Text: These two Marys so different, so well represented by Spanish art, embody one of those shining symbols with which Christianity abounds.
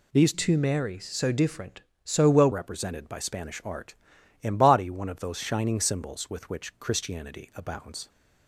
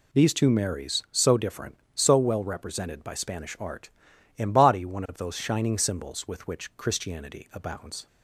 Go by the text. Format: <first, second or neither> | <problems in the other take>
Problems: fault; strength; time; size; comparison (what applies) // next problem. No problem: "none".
second | changes voice from "two" to "well"; from 0.3 to 2.5 s; 2.2 s long